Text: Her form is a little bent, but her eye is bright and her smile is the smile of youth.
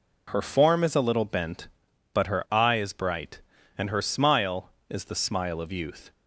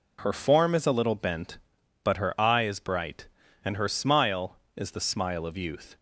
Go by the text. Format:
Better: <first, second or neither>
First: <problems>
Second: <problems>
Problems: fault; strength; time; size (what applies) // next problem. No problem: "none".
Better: neither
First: none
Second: none